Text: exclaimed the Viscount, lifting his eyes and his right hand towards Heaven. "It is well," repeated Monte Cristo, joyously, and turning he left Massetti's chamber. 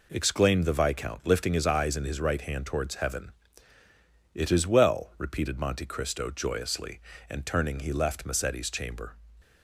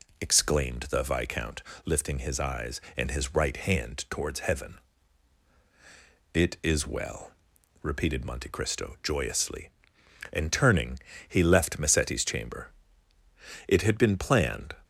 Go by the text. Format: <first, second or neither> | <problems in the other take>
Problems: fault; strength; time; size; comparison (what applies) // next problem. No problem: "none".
first | pauses between "turning" and "he"; slight; at 10.9 s; 0.30 s long // goes on to say "It had been planned"; noticeable; from 13.6 s on; 1.0 s long